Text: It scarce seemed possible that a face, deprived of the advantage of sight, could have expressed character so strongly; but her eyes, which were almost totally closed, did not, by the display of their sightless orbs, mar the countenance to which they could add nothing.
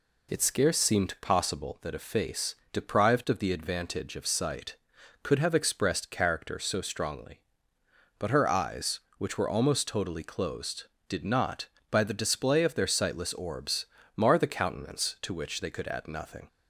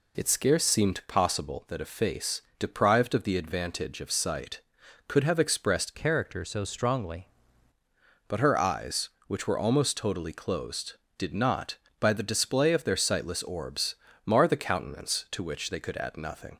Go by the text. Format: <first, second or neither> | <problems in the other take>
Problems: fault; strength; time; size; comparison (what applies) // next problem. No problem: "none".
first | changes voice from "character" to "strongly"; from 5.9 to 7.2 s; 1.3 s long